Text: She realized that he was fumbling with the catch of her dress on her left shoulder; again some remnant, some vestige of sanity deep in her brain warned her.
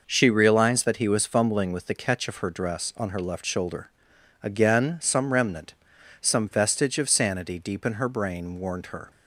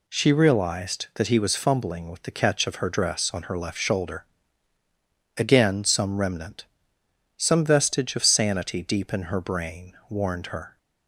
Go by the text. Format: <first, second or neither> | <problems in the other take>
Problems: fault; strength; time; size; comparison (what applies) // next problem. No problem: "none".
neither | none